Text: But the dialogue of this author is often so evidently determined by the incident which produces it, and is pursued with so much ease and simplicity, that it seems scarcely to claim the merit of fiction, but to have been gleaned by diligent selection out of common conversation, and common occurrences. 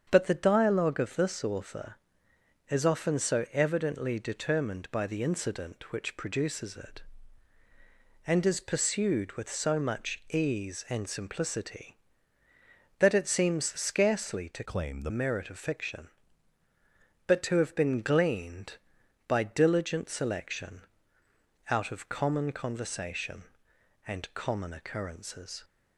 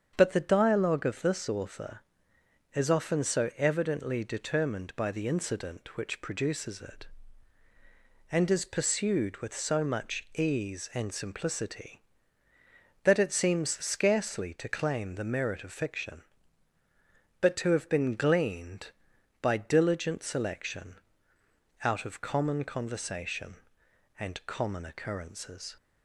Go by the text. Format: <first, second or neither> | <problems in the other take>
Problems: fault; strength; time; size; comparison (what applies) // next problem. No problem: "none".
second | starts louder than the rest; strong; until 1.1 s; 7.5 dB; strong in the second // changes voice from "claim" to "the"; from 14.6 to 15.1 s; 0.5 s long // pauses between "selection" and "out"; noticeable; at 20.8 s; 0.88 s long; noticeable in the second